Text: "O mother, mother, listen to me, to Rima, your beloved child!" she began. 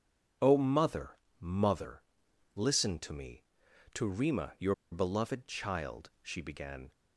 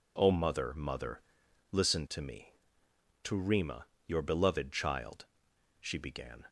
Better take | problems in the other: second | pauses between "your" and "beloved"; slight; at 4.7 s; 0.17 s long

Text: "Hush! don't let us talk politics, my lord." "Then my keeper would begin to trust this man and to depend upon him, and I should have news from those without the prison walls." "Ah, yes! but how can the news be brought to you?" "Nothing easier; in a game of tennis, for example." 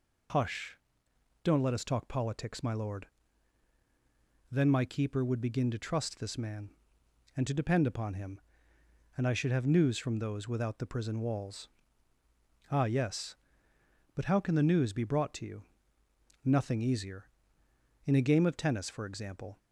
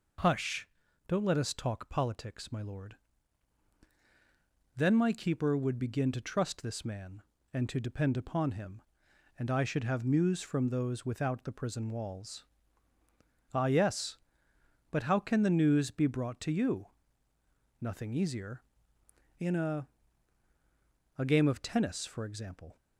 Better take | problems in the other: first | says "a" twice; at 21.1 s

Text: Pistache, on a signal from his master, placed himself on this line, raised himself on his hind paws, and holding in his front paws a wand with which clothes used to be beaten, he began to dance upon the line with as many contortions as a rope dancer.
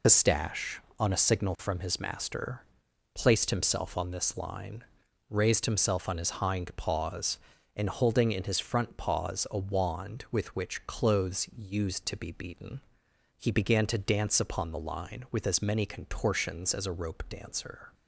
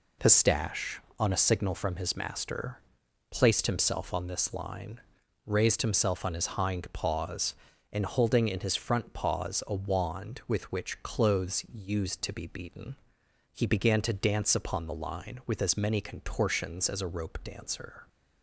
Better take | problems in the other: second | loses the start of "Pistache"; at 0.0 s; 50 ms

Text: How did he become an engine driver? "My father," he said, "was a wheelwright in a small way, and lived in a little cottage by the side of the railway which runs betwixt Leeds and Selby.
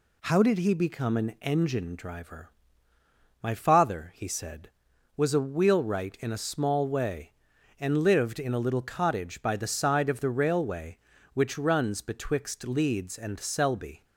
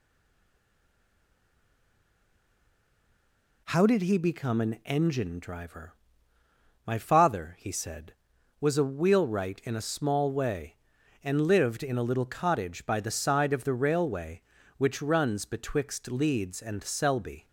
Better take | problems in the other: first | stays silent before the first word; strong; until 3.6 s; 3.6 s long

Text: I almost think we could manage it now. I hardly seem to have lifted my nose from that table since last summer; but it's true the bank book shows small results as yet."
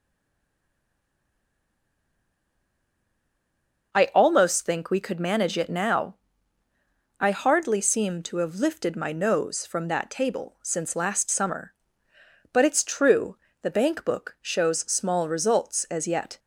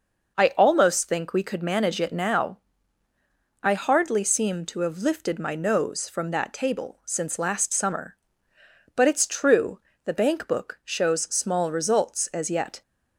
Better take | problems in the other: second | stays silent before the first word; strong; until 3.9 s; 3.9 s long // pauses between "true" and "the"; slight; at 13.3 s; 0.26 s long; slight in the second

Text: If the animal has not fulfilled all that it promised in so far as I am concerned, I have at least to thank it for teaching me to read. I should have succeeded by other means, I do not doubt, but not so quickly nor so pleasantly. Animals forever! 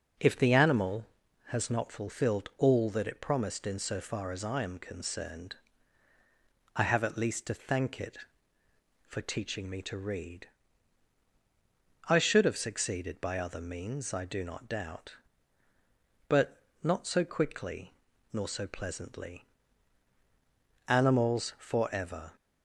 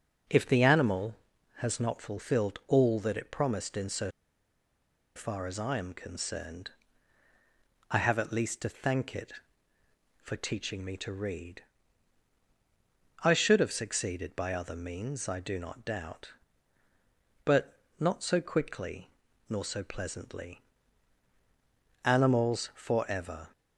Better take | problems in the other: first | pauses between "so" and "far"; at 4.1 s; 1.0 s long // pauses between "but" and "not"; slight; at 17.7 s; 0.22 s long; slight in the first // pauses between "quickly" and "nor"; at 19.0 s; 0.38 s long; also in the first

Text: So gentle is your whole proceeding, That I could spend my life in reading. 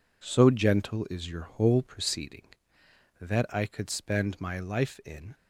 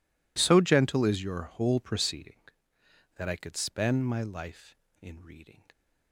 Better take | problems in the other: second | stops before "reading"; at 5.3 s

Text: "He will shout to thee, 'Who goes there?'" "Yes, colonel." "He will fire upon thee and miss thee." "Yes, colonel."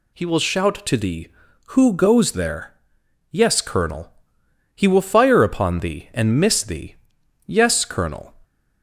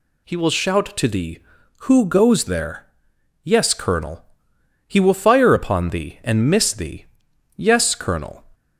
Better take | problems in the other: neither | none

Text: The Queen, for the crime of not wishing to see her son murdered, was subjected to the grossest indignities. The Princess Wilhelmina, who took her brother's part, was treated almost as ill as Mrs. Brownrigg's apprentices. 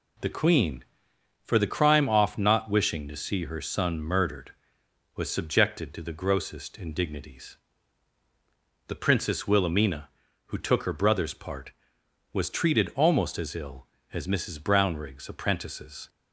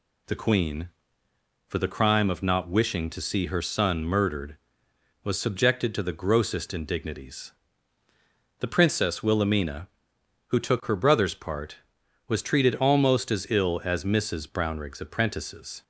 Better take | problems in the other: second | says "off" for "of"; at 2.0 s

